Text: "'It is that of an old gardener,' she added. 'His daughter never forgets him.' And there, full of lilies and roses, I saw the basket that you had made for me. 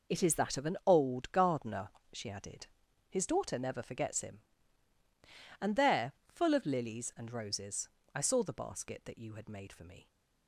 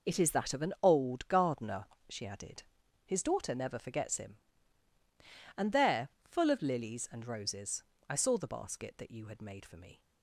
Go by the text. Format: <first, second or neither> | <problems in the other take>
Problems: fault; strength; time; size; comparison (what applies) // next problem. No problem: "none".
neither | none